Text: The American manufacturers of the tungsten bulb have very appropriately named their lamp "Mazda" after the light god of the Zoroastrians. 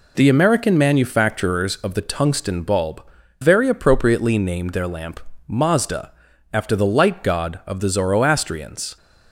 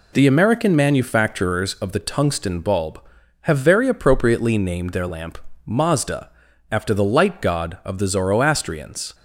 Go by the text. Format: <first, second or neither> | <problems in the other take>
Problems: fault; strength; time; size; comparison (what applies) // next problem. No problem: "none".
second | skips "have"; at 3.2 s // pauses between "lamp" and "Mazda"; slight; at 5.2 s; 0.26 s long; slight in the second // pauses between "Mazda" and "after"; at 6.1 s; 0.42 s long; also in the second